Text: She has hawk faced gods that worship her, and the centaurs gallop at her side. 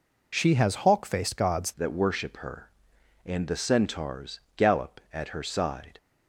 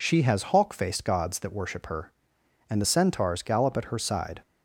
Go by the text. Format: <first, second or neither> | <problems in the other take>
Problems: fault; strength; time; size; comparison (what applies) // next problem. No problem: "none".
second | changes voice at "that"; from 1.7 s on; 4.2 s long // pauses between "centaurs" and "gallop"; slight; at 4.3 s; 0.16 s long